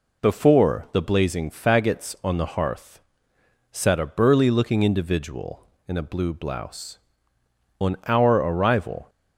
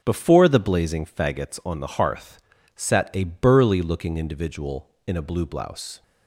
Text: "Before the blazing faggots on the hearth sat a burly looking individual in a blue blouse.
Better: second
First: pauses between "hearth" and "sat"; noticeable; at 2.9 s; 0.72 s long // goes on to say "On our arrival"; noticeable; from 7.7 s on; 1.3 s long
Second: pauses between "hearth" and "sat"; slight; at 2.4 s; 0.34 s long

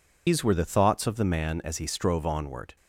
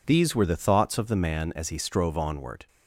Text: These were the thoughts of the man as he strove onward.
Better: second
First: loses the start of "These"; at 0.2 s; 145 ms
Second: none

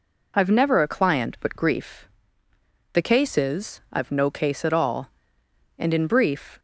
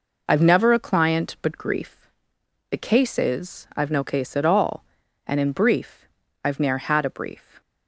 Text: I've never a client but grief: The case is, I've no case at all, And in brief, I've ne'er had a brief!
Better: second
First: stops before "I've ne'er had a brief"; at 6.5 s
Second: none

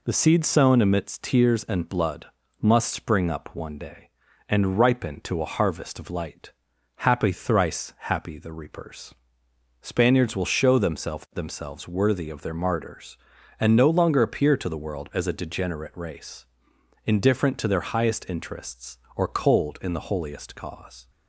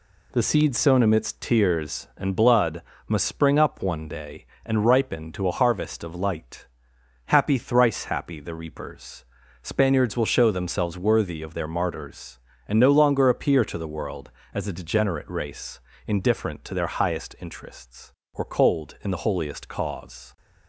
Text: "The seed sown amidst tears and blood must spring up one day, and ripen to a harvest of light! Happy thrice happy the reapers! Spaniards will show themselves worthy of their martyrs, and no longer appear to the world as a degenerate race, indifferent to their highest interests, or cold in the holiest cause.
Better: second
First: pauses between "blood" and "must"; slight; at 2.2 s; 0.34 s long // says "themselves" twice; at 11.3 s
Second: pauses between "blood" and "must"; slight; at 2.8 s; 0.26 s long

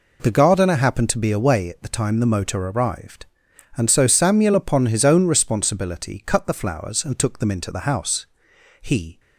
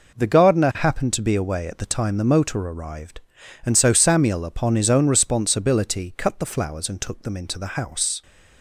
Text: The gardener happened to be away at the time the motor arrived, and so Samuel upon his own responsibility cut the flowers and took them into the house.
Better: second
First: goes on to say "He"; slight; from 8.8 s on; 0.38 s long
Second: none

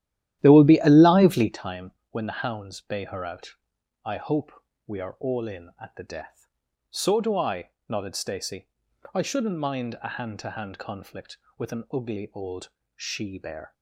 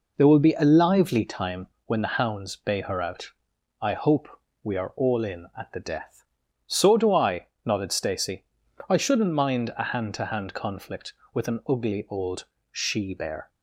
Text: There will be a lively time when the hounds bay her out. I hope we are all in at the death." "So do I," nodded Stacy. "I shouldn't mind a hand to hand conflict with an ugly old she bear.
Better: second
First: starts louder than the rest; strong; until 1.7 s; 12.5 dB // pauses between "time" and "when"; slight; at 1.9 s; 0.20 s long // pauses between "hope" and "we"; slight; at 4.5 s; 0.34 s long // pauses between "old" and "she"; slight; at 12.6 s; 0.26 s long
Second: pauses between "time" and "when"; slight; at 1.6 s; 0.20 s long // pauses between "hope" and "we"; slight; at 4.2 s; 0.34 s long // pauses between "old" and "she"; slight; at 12.4 s; 0.26 s long

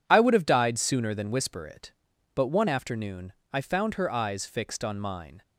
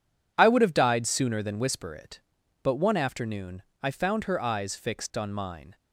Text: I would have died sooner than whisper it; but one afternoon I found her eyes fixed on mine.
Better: neither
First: pauses between "afternoon" and "I"; slight; at 3.3 s; 0.22 s long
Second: pauses between "afternoon" and "I"; slight; at 3.6 s; 0.22 s long

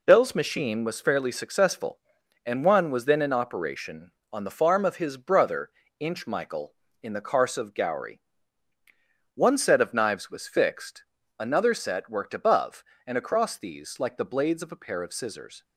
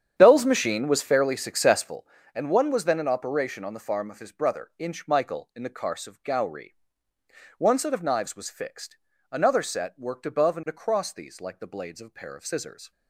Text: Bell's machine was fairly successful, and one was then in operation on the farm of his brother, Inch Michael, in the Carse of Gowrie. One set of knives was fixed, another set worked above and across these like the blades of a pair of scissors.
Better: first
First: none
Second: starts louder than the rest; strong; until 2.0 s; 9 dB

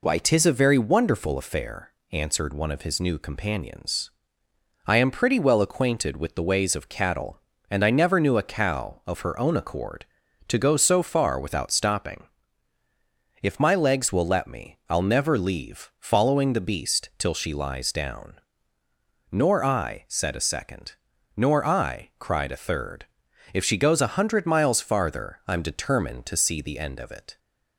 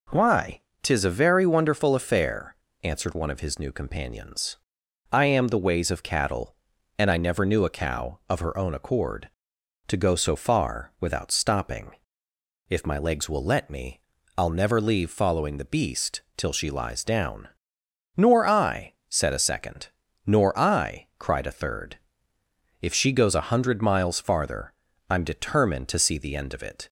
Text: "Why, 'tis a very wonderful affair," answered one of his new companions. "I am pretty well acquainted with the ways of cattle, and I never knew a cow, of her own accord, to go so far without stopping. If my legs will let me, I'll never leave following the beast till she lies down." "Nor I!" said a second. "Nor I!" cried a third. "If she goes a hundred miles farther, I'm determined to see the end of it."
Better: first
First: none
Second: skips "pretty well acquainted with"; at 5.4 s // pauses between "beast" and "till"; slight; at 16.2 s; 0.16 s long

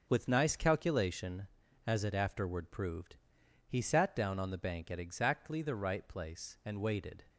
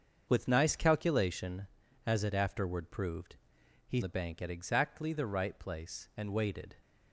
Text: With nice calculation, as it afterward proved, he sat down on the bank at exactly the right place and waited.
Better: first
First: none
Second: starts louder than the rest; until 1.2 s; 6.5 dB // skips "sat down on"; at 4.0 s

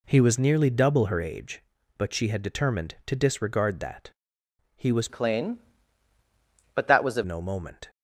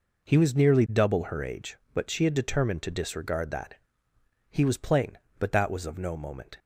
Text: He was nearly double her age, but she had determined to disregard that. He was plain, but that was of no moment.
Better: second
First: changes voice from "plain" to "of"; from 5.0 to 7.2 s; 2.2 s long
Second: none

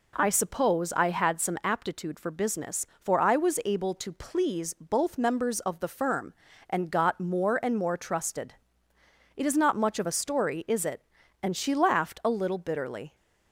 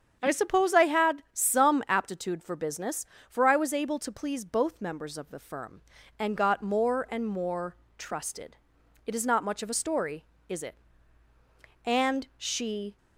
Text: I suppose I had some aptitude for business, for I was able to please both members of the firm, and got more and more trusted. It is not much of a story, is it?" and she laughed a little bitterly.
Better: first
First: none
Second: starts louder than the rest; strong; until 1.2 s; 7.5 dB // pauses between "more" and "trusted"; slight; at 7.7 s; 0.22 s long // stops before "laughed a little bitterly"; at 12.9 s

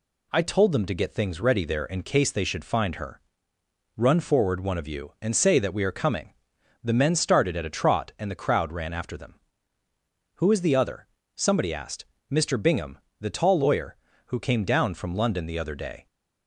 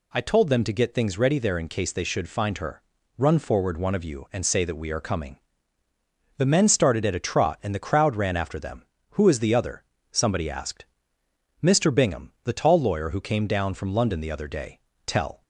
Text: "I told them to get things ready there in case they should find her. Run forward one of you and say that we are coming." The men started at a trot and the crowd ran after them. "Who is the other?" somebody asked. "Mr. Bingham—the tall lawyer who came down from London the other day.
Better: first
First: none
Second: goes on to say "Tell"; slight; from 15.0 s on; 0.36 s long

